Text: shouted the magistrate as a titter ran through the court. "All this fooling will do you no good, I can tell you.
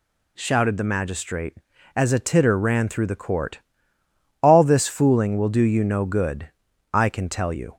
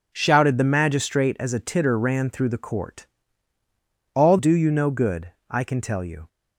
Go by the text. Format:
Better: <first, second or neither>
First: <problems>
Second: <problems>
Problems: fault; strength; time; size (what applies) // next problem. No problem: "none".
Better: first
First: none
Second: skips "this fooling will"; at 4.3 s